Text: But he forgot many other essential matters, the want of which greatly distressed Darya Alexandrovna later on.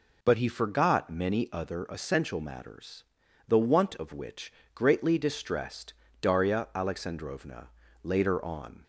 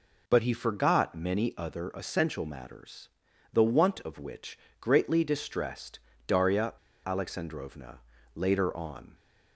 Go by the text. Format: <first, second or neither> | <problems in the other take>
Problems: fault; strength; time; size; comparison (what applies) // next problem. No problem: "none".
first | pauses between "which" and "greatly"; slight; at 4.5 s; 0.22 s long; slight in the first // pauses between "distressed" and "Darya"; slight; at 5.9 s; 0.26 s long; slight in the first // pauses between "Darya" and "Alexandrovna"; slight; at 6.7 s; 0.33 s long // pauses between "Alexandrovna" and "later"; slight; at 7.9 s; 0.36 s long; also in the first